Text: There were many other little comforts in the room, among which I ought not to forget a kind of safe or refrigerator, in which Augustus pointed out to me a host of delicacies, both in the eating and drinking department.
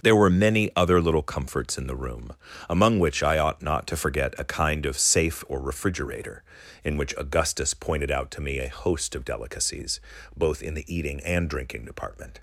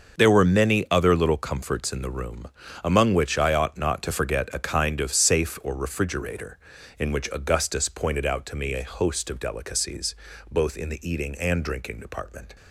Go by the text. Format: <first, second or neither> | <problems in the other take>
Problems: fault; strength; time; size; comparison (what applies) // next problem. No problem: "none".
neither | starts louder than the rest; the same in both